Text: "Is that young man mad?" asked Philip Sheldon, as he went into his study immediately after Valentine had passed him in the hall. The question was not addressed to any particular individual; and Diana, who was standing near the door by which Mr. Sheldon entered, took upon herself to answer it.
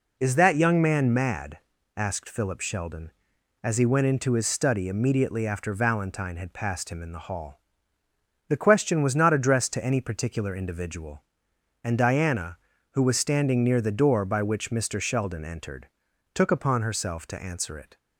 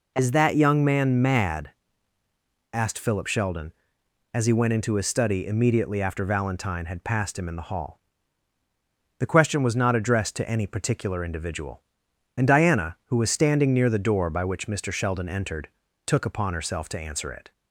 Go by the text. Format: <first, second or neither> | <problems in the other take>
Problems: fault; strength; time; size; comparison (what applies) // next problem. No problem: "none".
neither | none